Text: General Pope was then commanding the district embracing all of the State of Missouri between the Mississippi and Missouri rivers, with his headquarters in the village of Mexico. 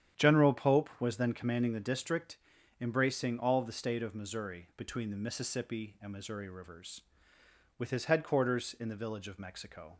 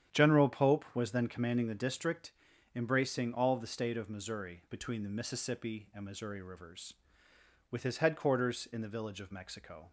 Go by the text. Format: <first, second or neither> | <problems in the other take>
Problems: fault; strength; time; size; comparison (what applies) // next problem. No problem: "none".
neither | starts louder than the rest; strong; the same in both // pauses between "district" and "embracing"; the same in both